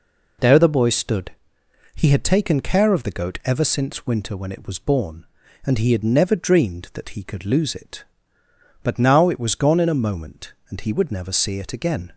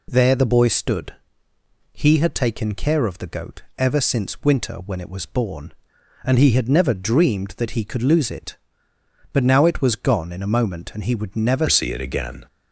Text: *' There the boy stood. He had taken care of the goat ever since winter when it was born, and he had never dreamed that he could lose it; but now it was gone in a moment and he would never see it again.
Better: first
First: none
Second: pauses between "goat" and "ever"; slight; at 3.6 s; 0.16 s long // changes voice at "see"; from 11.6 s on; 0.8 s long

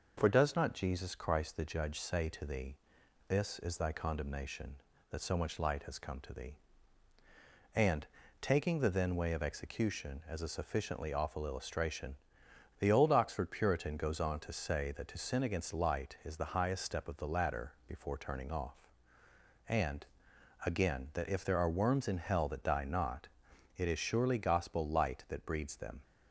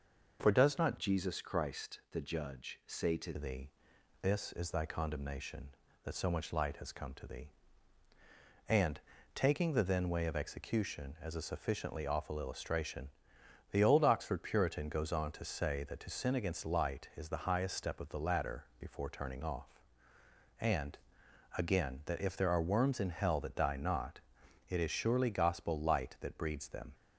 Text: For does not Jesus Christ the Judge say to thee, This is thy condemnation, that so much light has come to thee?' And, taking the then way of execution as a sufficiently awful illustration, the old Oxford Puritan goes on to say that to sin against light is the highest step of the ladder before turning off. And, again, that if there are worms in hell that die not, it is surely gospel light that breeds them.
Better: first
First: pauses between "ladder" and "before"; slight; at 17.7 s; 0.16 s long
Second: changes voice from "Jesus" to "to"; from 0.9 to 3.3 s; 2.4 s long // pauses between "ladder" and "before"; slight; at 18.6 s; 0.16 s long

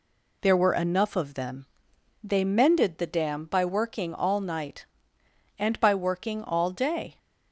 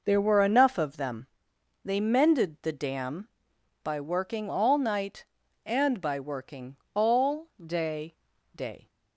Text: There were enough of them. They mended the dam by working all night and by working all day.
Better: first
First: none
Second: pauses between "working" and "all"; slight; at 6.7 s; 0.18 s long // pauses between "all" and "day"; slight; at 7.4 s; 0.16 s long // says "day" twice; at 8.5 s

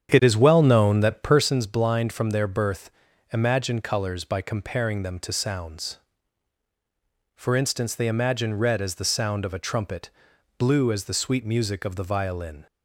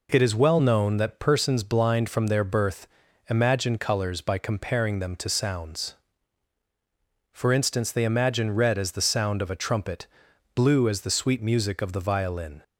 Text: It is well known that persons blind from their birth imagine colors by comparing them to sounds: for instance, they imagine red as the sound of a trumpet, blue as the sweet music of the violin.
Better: second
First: starts louder than the rest; strong; until 1.7 s; 8.5 dB // pauses between "birth" and "imagine"; at 2.9 s; 0.42 s long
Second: pauses between "birth" and "imagine"; at 2.8 s; 0.42 s long

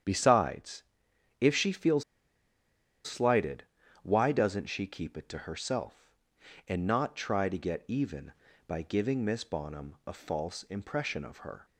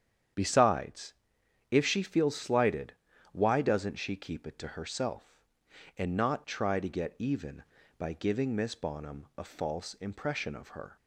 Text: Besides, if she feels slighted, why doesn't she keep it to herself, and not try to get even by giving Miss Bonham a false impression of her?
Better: second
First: starts louder than the rest; strong; until 1.6 s; 9 dB // pauses between "feels" and "slighted"; at 2.0 s; 1.0 s long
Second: starts louder than the rest; strong; until 1.9 s; 9 dB

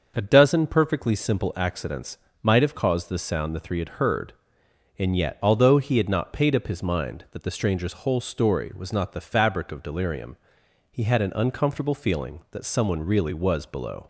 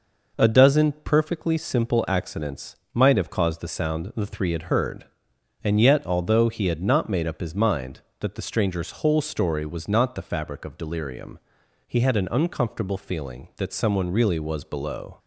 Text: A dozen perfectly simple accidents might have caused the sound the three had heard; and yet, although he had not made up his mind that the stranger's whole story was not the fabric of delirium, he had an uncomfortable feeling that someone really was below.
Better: second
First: starts louder than the rest; until 1.1 s; 6.5 dB // pauses between "accidents" and "might"; slight; at 2.1 s; 0.24 s long // says "paid" for "made"; at 6.3 s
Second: pauses between "accidents" and "might"; slight; at 2.7 s; 0.18 s long

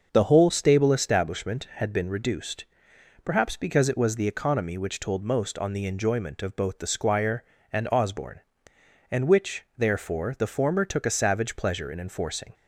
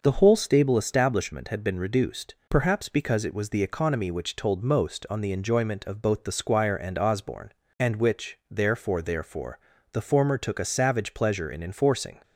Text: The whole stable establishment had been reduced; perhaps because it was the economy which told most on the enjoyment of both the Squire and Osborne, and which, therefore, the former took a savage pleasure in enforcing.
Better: first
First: starts louder than the rest; until 1.1 s; 6 dB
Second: starts louder than the rest; noticeable; until 1.0 s; 6 dB // says "therefore" twice; at 9.0 s

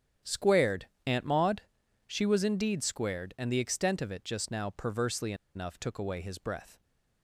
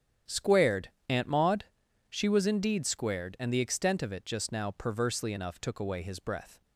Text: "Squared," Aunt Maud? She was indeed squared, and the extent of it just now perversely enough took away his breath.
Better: second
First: starts louder than the rest; strong; until 1.4 s; 9.5 dB // pauses between "perversely" and "enough"; slight; at 5.3 s; 0.21 s long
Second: starts louder than the rest; strong; until 1.4 s; 9.5 dB

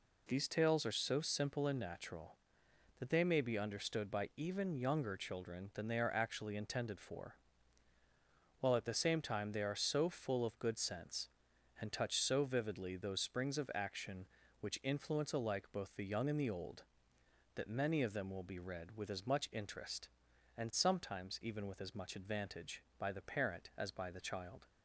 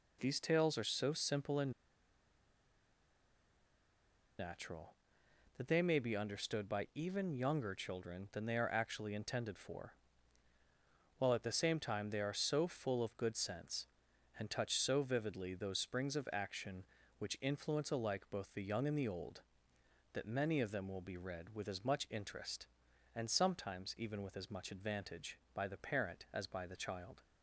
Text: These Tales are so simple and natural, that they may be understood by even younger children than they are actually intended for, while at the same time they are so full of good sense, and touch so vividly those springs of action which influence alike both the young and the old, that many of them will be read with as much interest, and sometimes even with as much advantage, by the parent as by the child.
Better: first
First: none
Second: pauses between "and" and "natural"; strong; at 1.7 s; 2.6 s long

